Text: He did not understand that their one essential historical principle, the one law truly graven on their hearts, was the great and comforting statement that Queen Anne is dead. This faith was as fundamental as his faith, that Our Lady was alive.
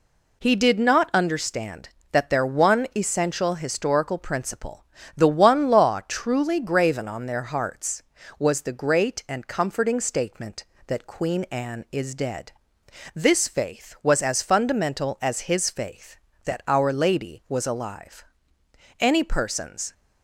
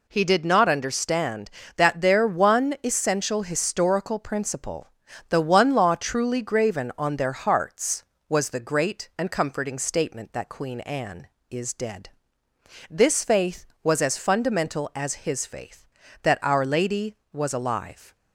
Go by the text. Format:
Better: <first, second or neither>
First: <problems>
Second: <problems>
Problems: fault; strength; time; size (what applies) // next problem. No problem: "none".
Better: second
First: goes on to say "Any persons"; noticeable; from 19.0 s on; 0.92 s long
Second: none